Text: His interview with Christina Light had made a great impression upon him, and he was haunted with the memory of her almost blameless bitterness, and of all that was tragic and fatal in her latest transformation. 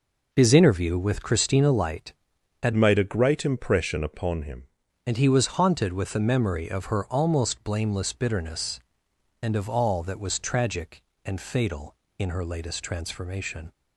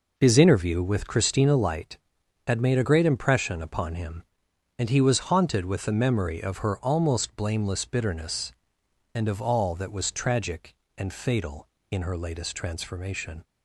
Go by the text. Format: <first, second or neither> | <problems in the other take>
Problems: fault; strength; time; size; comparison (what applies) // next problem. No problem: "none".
second | changes voice from "made" to "him"; from 2.7 to 4.6 s; 1.9 s long